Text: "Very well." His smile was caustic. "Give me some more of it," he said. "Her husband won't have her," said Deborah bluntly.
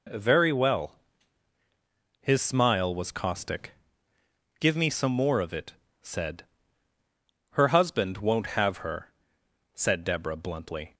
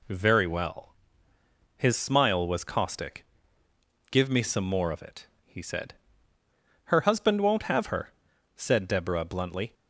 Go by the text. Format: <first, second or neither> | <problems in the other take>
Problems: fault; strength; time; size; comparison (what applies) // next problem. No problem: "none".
second | skips "he"; at 5.8 s